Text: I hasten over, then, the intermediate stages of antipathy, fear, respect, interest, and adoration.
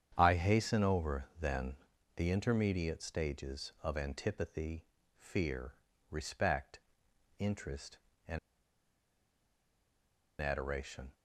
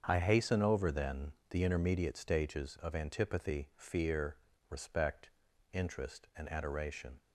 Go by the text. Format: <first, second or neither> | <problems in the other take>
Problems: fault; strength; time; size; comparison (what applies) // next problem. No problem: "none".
second | starts louder than the rest; strong; until 1.1 s; 8.5 dB; strong in the second // pauses between "and" and "adoration"; strong; at 8.3 s; 2.0 s long